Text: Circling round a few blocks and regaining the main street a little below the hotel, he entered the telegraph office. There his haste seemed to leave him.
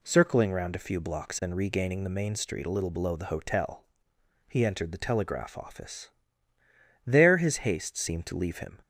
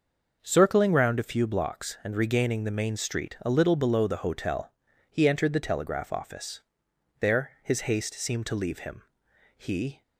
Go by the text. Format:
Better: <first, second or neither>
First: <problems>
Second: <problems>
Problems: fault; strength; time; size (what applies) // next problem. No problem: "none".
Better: first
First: none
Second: starts louder than the rest; noticeable; until 1.4 s; 6 dB // goes on to say "He"; slight; from 9.5 s on; 0.46 s long